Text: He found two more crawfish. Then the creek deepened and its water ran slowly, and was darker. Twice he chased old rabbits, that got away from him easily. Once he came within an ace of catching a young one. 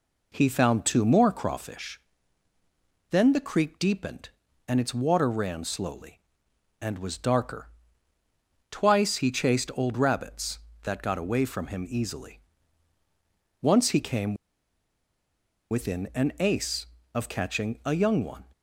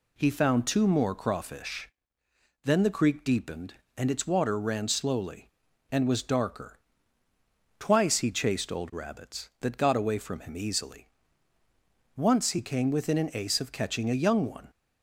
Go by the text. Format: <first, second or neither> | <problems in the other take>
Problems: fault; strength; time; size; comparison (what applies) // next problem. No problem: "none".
second | pauses between "came" and "within"; strong; at 14.3 s; 1.3 s long